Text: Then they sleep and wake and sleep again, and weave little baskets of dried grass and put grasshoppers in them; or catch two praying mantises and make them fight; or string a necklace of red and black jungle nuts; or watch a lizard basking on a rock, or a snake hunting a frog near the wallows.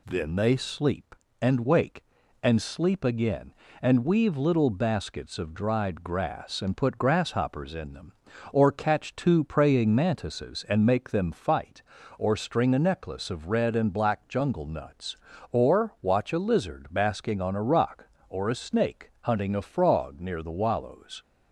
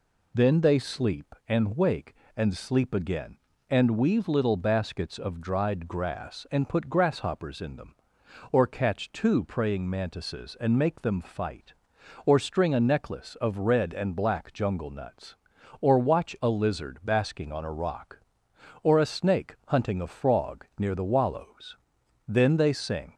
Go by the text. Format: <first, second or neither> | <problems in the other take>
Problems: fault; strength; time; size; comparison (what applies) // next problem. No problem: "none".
first | goes on to say "Then they sing"; noticeable; from 22.2 s on; 0.88 s long